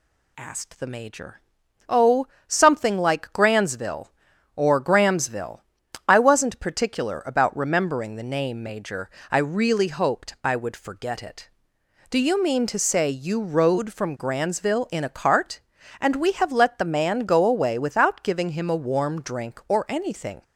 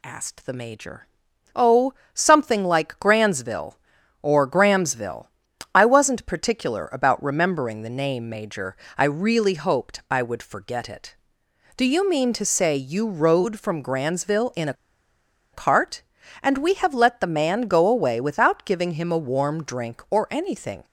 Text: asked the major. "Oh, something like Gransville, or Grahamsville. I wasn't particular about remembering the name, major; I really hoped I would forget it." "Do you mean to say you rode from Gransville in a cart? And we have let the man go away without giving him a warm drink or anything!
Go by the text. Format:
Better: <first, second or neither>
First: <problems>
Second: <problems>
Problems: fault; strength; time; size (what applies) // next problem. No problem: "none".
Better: first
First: none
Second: pauses between "a" and "cart"; noticeable; at 14.7 s; 0.79 s long